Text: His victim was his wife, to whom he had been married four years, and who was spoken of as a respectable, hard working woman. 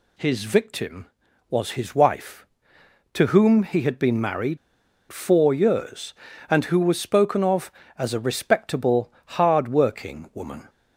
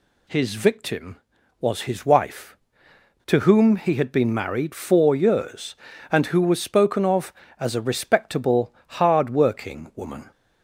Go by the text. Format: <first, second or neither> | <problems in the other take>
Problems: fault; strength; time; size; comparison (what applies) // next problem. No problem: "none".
second | pauses between "married" and "four"; noticeable; at 4.5 s; 0.53 s long